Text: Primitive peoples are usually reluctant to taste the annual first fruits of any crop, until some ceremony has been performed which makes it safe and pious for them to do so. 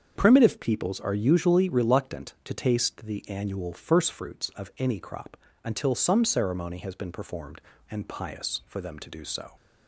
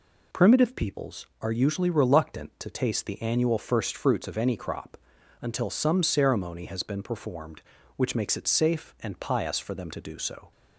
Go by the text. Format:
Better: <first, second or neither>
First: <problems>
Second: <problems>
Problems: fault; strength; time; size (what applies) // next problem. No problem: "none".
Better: second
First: starts louder than the rest; until 1.1 s; 7 dB // skips "which makes it safe"; at 7.7 s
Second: none